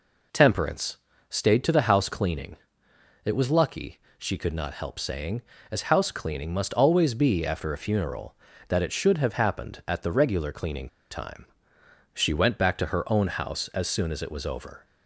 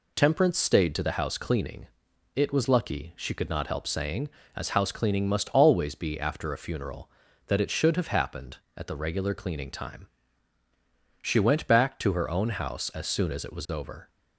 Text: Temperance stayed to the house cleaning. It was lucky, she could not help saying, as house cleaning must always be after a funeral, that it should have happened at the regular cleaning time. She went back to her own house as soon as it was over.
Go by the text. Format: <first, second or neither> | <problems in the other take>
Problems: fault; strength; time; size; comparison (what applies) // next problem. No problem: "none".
second | pauses between "Temperance" and "stayed"; slight; at 0.9 s; 0.30 s long // pauses between "cleaning" and "time"; slight; at 10.8 s; 0.22 s long